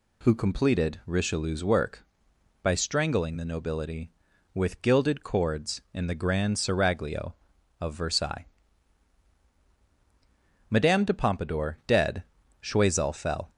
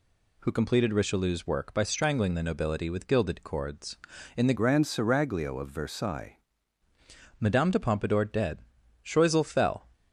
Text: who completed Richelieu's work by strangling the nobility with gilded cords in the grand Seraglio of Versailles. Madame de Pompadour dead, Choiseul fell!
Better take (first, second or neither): first